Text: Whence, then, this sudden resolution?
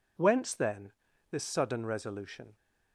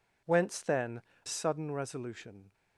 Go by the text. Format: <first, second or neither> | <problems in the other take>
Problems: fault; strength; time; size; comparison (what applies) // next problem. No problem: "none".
first | skips "this"; at 1.1 s